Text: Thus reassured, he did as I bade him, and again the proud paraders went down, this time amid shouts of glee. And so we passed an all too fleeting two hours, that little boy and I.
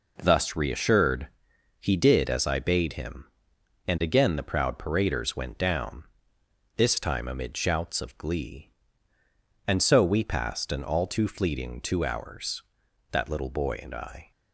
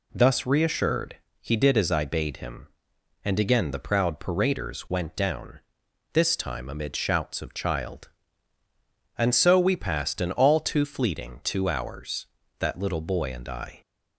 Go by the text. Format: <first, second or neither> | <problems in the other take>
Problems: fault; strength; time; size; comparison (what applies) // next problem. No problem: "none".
first | says "child" for "glee"; at 7.5 s